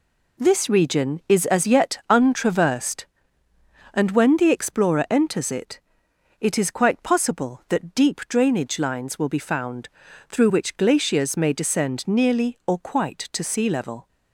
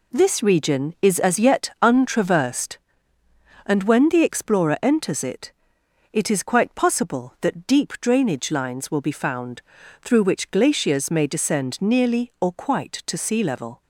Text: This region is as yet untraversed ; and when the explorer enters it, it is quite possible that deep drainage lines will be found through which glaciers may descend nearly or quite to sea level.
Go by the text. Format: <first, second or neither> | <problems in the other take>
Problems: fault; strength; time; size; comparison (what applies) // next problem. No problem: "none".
neither | pauses between "found" and "through"; the same in both